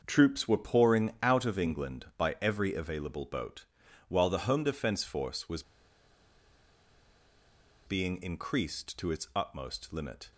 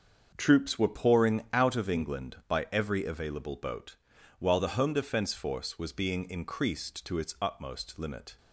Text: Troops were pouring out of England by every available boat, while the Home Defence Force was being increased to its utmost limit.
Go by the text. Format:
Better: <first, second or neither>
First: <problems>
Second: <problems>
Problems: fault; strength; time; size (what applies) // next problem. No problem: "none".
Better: second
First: starts louder than the rest; until 1.0 s; 6.5 dB // pauses between "was" and "being"; strong; at 5.6 s; 2.2 s long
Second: starts louder than the rest; until 1.3 s; 6.5 dB